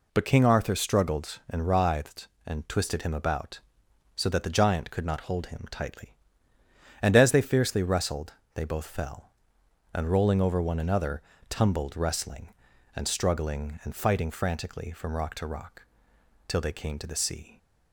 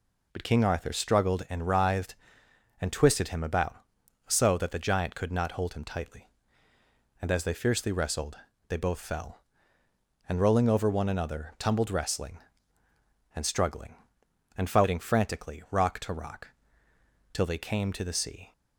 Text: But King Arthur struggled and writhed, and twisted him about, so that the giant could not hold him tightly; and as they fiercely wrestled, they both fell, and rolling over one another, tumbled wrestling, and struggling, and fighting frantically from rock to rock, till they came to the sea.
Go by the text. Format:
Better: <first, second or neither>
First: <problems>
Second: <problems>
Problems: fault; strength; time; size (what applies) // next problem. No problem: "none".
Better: first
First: none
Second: skips "from"; at 15.6 s